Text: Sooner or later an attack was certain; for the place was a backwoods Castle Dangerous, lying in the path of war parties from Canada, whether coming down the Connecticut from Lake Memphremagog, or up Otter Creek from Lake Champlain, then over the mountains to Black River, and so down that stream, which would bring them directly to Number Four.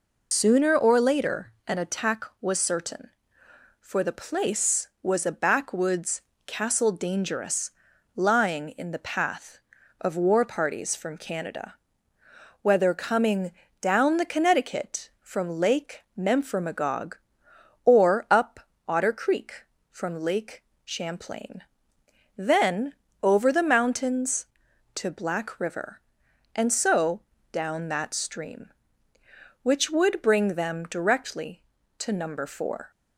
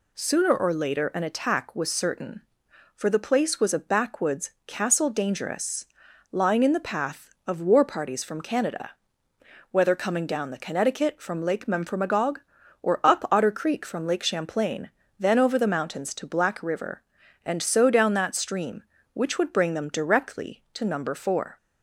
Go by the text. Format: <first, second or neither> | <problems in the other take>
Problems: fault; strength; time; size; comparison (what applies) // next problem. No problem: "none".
second | loses the start of "Sooner"; at 0.3 s; 125 ms // pauses between "backwoods" and "Castle"; slight; at 6.2 s; 0.22 s long; slight in the second // pauses between "coming" and "down"; slight; at 13.5 s; 0.28 s long // pauses between "Lake" and "Memphremagog"; slight; at 16.0 s; 0.18 s long // pauses between "up" and "Otter"; slight; at 18.6 s; 0.22 s long // pauses between "Lake" and "Champlain"; slight; at 20.6 s; 0.20 s long // pauses between "then" and "over"; slight; at 22.9 s; 0.30 s long // pauses between "so" and "down"; slight; at 27.2 s; 0.32 s long